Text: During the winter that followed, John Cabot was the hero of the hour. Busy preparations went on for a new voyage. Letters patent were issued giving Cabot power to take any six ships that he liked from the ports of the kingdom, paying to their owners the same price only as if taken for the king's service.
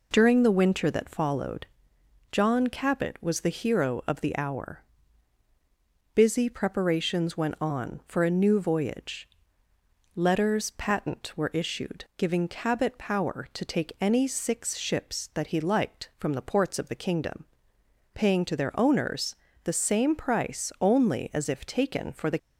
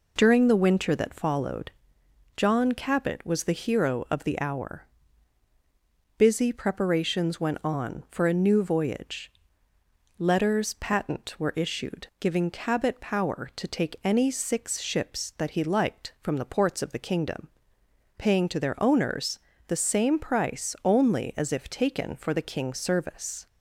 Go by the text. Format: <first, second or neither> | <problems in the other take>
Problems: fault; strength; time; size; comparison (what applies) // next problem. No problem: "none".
second | pauses between "owners" and "the"; slight; at 19.3 s; 0.26 s long; slight in the second // stops before "king's service"; at 22.3 s